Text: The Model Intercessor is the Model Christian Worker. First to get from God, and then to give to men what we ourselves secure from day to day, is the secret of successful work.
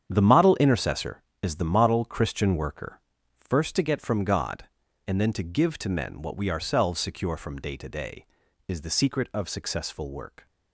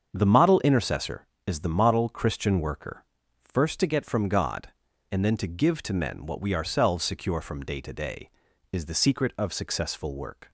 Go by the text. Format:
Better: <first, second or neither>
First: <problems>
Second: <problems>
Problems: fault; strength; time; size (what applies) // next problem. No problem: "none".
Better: second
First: gets quieter; strong; throughout; 10 dB // starts louder than the rest; strong; until 1.1 s; 8.5 dB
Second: starts louder than the rest; strong; until 1.1 s; 7 dB